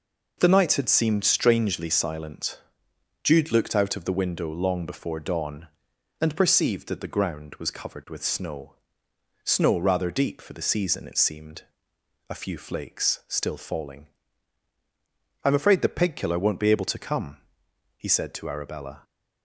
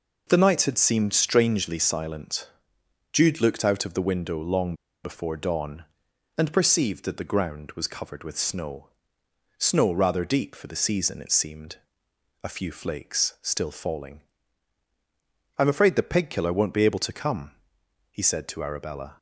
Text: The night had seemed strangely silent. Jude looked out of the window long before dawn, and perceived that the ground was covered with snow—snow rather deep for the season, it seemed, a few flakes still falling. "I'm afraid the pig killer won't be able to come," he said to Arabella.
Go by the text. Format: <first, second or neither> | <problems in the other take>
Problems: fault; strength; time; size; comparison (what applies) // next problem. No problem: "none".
first | pauses between "long" and "before"; slight; at 4.7 s; 0.30 s long